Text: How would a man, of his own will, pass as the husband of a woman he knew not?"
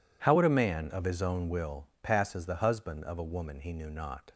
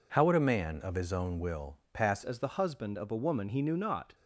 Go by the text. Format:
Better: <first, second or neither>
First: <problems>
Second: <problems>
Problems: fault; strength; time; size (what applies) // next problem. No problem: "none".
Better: first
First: none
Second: changes voice at "as"; from 2.2 s on; 1.9 s long